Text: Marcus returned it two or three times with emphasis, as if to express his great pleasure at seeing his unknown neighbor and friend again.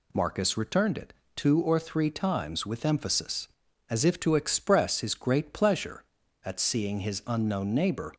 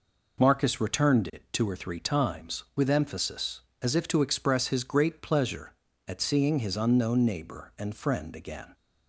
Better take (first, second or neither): second